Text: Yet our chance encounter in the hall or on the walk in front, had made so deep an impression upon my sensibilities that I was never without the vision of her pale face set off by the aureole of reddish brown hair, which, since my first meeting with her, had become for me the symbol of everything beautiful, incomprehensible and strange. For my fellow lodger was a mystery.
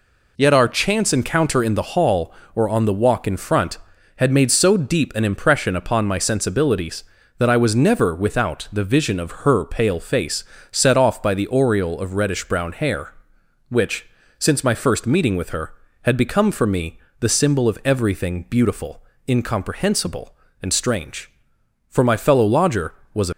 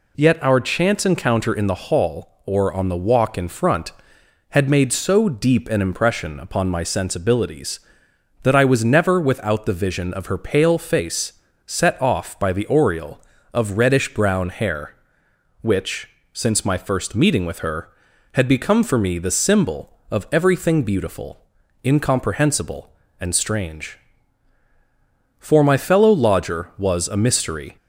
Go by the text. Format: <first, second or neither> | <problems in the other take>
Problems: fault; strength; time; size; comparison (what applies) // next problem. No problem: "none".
second | pauses between "face" and "set"; slight; at 10.4 s; 0.30 s long; slight in the second // pauses between "me" and "the"; slight; at 16.9 s; 0.22 s long // stops before "mystery"; at 23.3 s